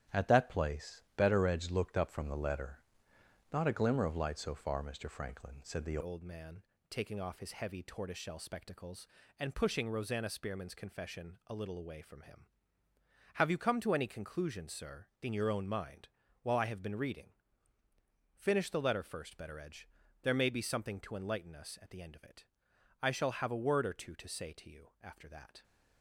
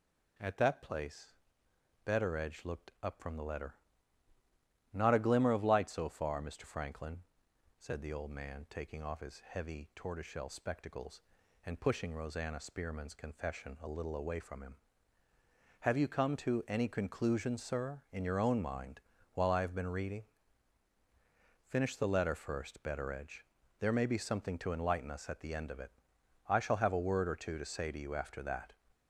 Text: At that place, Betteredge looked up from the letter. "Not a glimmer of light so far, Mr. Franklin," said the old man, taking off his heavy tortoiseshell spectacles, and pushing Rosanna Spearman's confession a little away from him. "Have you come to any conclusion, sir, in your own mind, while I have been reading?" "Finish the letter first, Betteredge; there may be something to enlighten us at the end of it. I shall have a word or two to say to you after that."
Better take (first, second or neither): second